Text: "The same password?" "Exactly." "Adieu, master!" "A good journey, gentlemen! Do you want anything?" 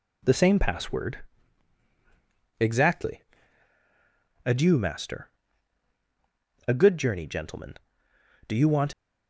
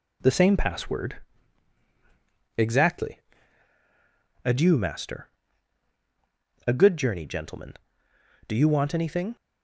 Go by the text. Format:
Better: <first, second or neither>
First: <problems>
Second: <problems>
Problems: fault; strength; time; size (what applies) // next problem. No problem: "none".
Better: second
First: stops before "anything"; at 8.9 s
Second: none